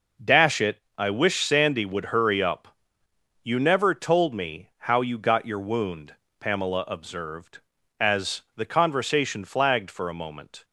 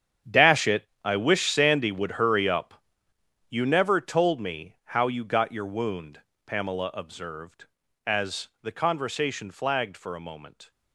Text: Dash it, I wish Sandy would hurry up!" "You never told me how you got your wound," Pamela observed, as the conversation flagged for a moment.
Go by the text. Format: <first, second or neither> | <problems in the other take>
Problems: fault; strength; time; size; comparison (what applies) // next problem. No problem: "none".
first | gets quieter; strong; throughout; 13.5 dB